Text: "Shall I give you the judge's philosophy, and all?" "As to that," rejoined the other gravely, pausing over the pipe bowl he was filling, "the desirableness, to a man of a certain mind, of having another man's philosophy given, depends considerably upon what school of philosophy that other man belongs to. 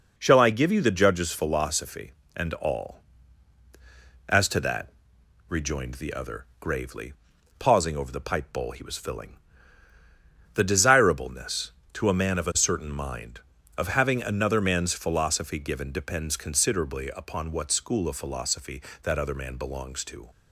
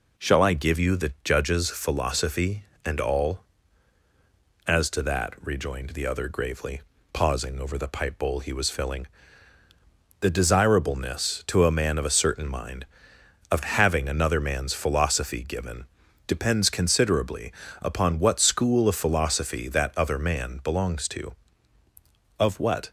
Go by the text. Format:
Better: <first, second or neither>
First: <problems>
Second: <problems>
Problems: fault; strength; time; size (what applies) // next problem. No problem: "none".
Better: first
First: none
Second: pauses between "considerably" and "upon"; slight; at 17.5 s; 0.30 s long // goes on to say "Of what"; from 22.3 s on; 0.52 s long